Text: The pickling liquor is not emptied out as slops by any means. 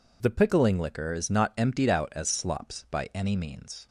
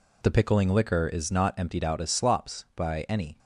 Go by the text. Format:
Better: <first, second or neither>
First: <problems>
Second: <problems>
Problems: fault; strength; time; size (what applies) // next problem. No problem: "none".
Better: first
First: none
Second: stops before "means"; at 3.3 s